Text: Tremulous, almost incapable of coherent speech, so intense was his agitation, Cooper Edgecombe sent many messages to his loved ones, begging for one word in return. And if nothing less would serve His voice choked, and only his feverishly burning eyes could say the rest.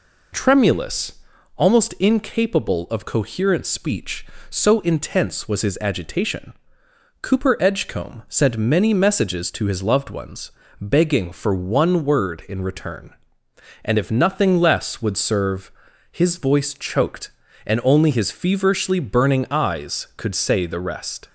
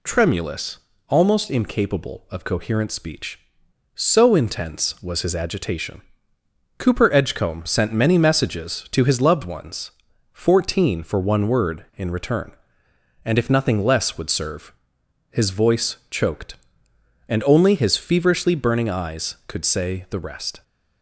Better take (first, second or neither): first